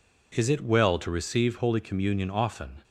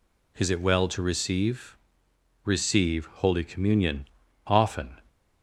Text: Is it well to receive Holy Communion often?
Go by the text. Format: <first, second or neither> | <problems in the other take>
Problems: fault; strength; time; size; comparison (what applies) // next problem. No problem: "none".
first | says "receive" twice; at 2.4 s // pauses between "Communion" and "often"; at 4.0 s; 0.40 s long